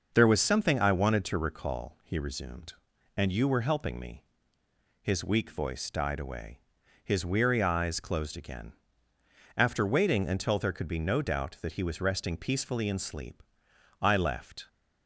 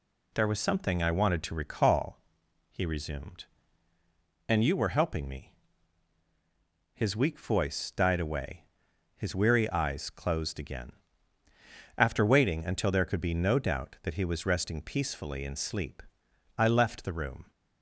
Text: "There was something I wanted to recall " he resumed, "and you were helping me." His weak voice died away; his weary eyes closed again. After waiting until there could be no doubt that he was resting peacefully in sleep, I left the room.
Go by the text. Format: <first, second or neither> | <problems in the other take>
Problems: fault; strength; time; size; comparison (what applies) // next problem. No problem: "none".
second | stops before "the room"; at 14.6 s